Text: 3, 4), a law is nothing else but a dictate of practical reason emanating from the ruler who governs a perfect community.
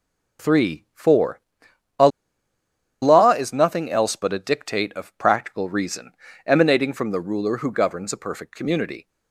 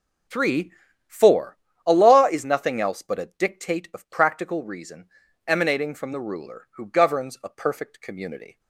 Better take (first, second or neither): second